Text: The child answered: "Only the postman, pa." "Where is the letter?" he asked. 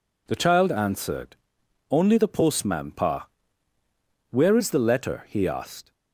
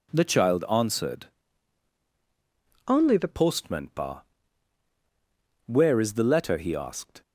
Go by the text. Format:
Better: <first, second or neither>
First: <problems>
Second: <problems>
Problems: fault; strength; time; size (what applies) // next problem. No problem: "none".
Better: first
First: none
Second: changes voice from "Only" to "the"; from 2.8 to 3.2 s; 0.4 s long